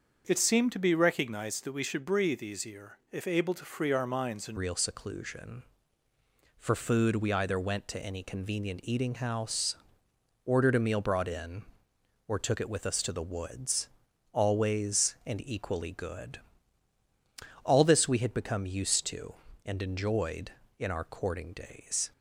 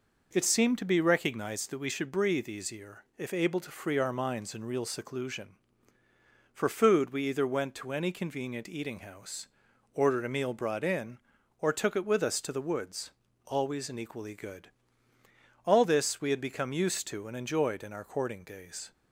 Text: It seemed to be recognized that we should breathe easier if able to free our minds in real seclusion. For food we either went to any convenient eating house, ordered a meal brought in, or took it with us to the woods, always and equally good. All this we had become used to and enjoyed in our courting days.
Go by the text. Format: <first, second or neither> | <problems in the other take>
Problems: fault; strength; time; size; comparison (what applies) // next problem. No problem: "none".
second | starts louder than the rest; until 1.2 s; 6.5 dB // changes voice at "real"; from 4.5 s on; 17.6 s long